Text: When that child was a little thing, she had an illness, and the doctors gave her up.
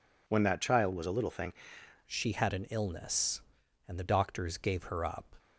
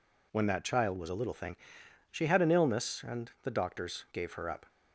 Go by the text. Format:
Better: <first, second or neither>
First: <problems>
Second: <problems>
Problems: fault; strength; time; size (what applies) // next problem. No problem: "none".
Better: second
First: changes voice at "she"; from 2.0 s on; 3.3 s long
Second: none